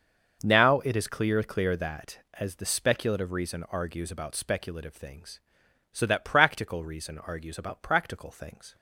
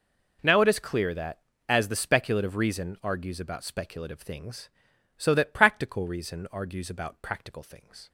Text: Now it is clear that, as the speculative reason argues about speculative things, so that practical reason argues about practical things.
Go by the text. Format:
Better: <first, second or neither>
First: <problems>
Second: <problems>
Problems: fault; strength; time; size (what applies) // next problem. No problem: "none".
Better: second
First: starts louder than the rest; noticeable; until 1.4 s; 6 dB // says "clear" twice; at 1.4 s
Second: none